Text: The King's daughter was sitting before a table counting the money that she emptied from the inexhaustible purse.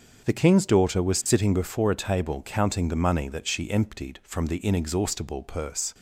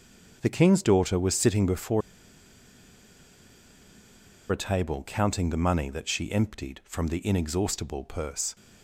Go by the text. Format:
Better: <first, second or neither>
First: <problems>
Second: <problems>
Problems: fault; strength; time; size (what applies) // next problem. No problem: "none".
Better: first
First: starts louder than the rest; until 1.2 s; 7 dB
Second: starts louder than the rest; until 1.4 s; 7 dB // pauses between "before" and "a"; strong; at 2.0 s; 2.5 s long